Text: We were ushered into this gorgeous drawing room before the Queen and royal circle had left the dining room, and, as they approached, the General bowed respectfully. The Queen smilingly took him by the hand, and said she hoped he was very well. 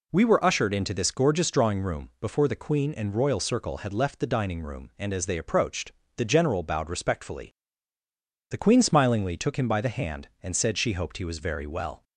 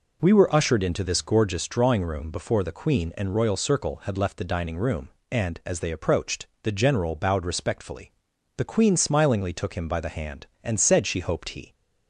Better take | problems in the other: first | stops before "was very well"; at 11.7 s

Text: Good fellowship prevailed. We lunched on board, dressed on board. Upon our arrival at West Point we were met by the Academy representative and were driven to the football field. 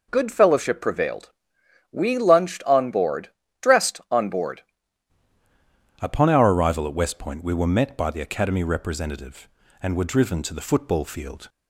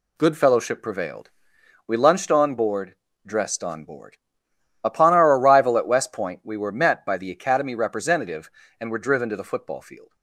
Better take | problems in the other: second | changes voice at "Upon"; from 6.0 s on; 5.4 s long

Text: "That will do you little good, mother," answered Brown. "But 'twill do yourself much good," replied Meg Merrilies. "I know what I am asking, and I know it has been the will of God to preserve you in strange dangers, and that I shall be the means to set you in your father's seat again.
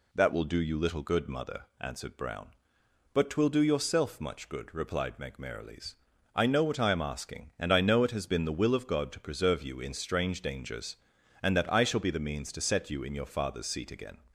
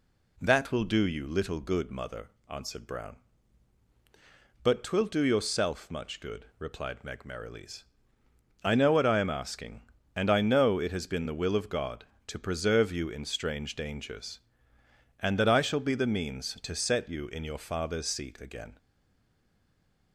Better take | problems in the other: first | stays silent after the last word; noticeable; from 18.7 s on; 1.4 s long

